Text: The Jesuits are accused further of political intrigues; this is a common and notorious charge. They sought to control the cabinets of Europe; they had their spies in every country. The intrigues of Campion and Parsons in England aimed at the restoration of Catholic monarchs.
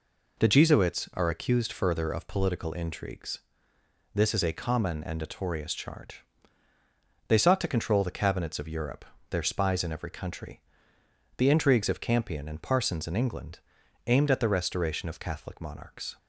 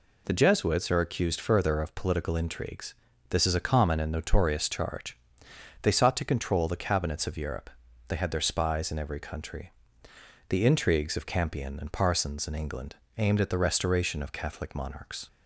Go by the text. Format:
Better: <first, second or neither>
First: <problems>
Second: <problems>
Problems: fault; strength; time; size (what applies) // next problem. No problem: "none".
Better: second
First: skips "they had"; at 9.1 s // pauses between "England" and "aimed"; noticeable; at 13.5 s; 0.48 s long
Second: pauses between "England" and "aimed"; slight; at 12.9 s; 0.22 s long